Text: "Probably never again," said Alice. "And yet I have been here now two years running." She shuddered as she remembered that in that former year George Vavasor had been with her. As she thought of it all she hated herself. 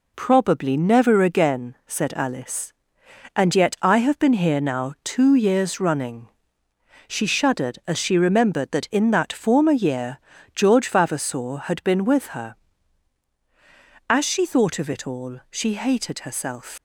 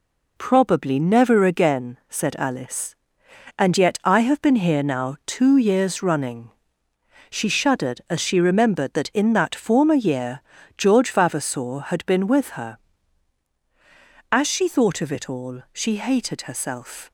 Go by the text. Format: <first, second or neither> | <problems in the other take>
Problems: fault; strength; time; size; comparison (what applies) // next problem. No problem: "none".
second | pauses between "year" and "George"; slight; at 10.1 s; 0.36 s long; slight in the second // leaves "herself" unfinished; at 16.7 s; 110 ms